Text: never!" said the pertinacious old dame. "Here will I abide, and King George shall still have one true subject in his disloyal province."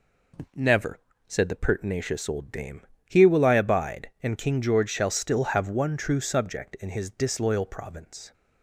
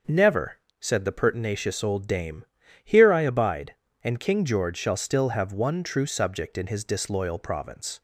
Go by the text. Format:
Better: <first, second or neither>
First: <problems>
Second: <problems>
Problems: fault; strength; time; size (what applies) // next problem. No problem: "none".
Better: first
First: none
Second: starts louder than the rest; until 1.3 s; 6 dB // skips "will"; at 3.1 s